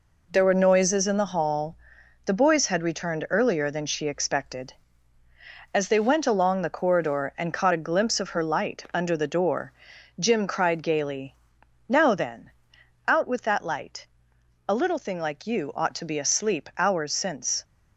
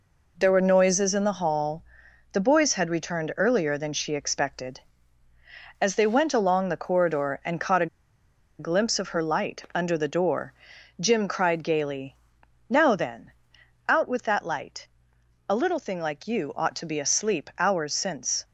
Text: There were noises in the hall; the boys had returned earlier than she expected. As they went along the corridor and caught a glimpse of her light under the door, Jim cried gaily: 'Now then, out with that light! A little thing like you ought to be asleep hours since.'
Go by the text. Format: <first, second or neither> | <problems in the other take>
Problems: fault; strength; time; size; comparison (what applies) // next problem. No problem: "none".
first | pauses between "a" and "glimpse"; noticeable; at 7.8 s; 0.72 s long